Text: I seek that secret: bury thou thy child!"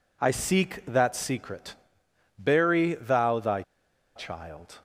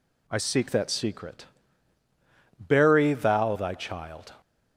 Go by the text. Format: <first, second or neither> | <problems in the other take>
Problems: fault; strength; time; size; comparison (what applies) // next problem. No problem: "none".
second | pauses between "thy" and "child"; noticeable; at 3.6 s; 0.54 s long